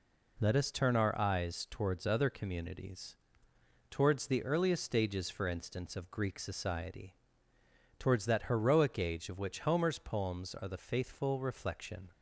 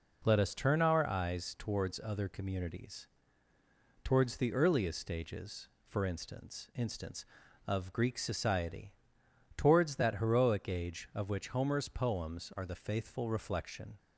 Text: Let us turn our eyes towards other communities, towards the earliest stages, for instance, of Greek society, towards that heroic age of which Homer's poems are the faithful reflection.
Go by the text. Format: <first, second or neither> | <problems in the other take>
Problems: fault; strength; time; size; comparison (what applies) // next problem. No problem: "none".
first | says "instance" twice; at 6.7 s